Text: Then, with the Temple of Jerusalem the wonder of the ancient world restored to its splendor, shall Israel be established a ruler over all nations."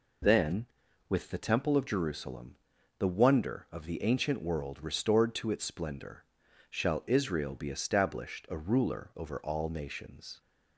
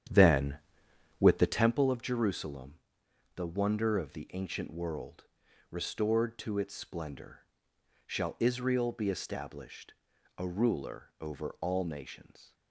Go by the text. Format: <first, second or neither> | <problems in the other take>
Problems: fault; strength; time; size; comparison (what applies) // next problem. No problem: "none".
first | starts louder than the rest; strong; until 1.8 s; 9.5 dB // pauses between "Jerusalem" and "the"; noticeable; at 2.7 s; 0.56 s long; also in the first // pauses between "world" and "restored"; at 5.2 s; 0.44 s long // pauses between "established" and "a"; noticeable; at 9.9 s; 0.46 s long